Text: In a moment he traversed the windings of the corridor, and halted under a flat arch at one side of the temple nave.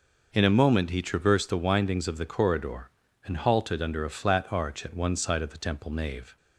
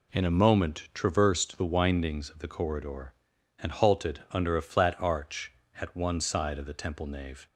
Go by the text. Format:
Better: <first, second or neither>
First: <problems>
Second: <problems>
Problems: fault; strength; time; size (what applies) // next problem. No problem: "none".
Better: first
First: none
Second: skips "he"; at 0.9 s